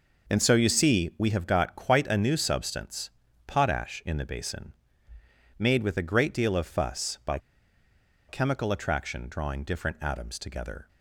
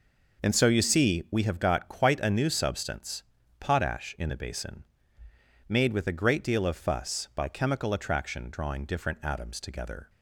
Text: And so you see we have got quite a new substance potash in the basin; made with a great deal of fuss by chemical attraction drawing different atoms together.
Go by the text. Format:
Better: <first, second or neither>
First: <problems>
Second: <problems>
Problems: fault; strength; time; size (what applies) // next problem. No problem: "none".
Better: second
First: pauses between "substance" and "potash"; at 3.0 s; 0.38 s long // pauses between "by" and "chemical"; noticeable; at 7.3 s; 0.91 s long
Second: pauses between "substance" and "potash"; at 3.2 s; 0.38 s long